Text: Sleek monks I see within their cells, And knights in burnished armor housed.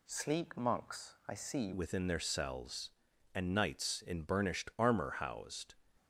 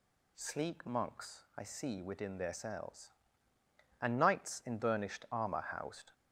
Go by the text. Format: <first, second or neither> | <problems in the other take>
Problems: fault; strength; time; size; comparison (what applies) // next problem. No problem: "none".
second | changes voice at "within"; from 1.7 s on; 4.0 s long